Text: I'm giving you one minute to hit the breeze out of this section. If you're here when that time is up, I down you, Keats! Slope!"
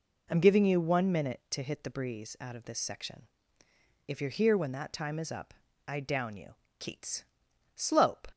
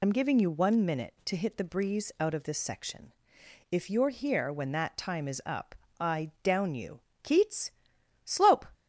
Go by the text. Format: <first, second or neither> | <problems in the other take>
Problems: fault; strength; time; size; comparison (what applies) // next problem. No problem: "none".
first | loses the start of "I'm"; at 0.0 s; 65 ms